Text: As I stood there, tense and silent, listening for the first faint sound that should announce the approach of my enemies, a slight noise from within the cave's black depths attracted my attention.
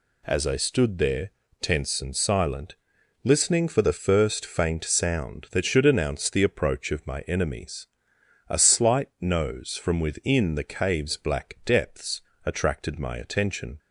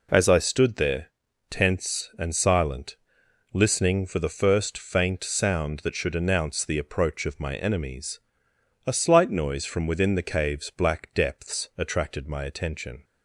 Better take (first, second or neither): second